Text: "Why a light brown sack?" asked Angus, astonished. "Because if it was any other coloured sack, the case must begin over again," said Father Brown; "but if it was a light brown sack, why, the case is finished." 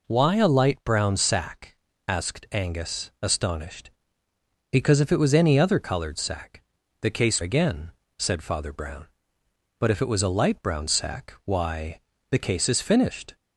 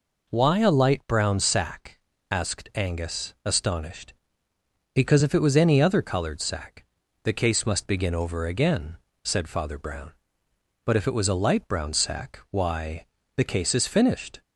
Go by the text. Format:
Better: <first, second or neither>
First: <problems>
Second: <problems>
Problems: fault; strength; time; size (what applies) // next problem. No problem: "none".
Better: second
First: skips "must begin over"; at 7.4 s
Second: none